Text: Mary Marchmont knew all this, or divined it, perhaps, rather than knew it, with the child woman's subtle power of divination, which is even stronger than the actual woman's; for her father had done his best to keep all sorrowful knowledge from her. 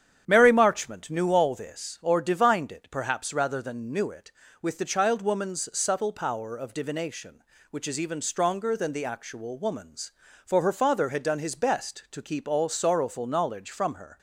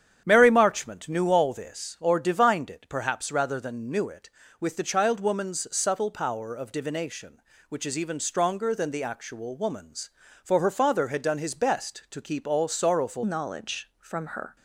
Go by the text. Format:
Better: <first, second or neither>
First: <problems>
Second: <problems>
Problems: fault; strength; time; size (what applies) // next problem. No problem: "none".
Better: first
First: starts louder than the rest; strong; until 1.2 s; 9 dB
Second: starts louder than the rest; strong; until 1.2 s; 9 dB // changes voice at "knowledge"; from 13.2 s on; 1.3 s long